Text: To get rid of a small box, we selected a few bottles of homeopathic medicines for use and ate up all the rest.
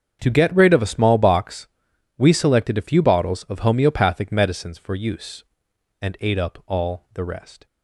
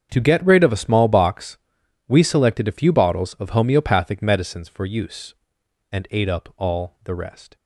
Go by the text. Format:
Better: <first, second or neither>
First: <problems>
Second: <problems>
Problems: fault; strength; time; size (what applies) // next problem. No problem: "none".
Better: neither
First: starts louder than the rest; strong; until 1.2 s; 7.5 dB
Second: starts louder than the rest; strong; until 1.1 s; 7.5 dB